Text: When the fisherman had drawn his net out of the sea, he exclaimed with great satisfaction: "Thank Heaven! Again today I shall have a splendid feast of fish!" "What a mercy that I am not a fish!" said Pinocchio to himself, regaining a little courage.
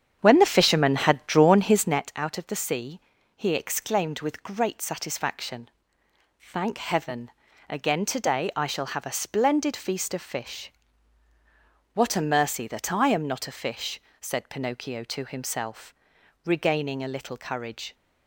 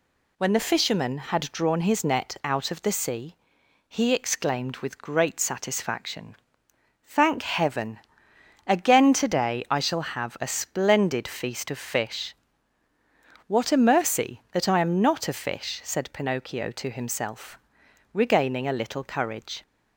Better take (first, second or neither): second